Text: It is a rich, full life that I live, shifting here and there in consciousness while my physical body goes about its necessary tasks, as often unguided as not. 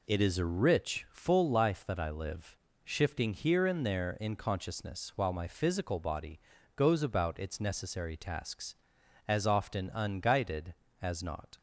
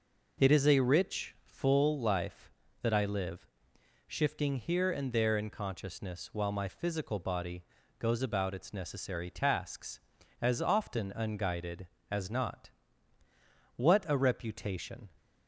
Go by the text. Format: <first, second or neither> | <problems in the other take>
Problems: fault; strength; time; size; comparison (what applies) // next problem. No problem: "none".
first | pauses between "body" and "goes"; slight; at 7.6 s; 0.34 s long; slight in the first // goes on to say "What a reputation"; from 13.7 s on; 1.3 s long